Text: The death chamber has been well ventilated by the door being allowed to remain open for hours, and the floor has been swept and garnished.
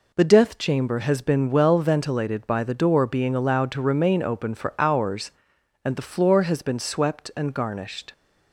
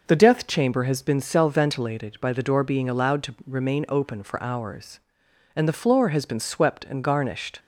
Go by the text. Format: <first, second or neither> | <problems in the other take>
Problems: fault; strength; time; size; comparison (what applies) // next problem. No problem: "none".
first | says "cell" for "well"; at 1.1 s